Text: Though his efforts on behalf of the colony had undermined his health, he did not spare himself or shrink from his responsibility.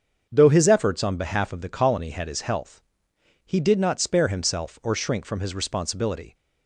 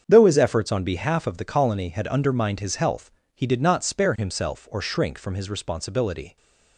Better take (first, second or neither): second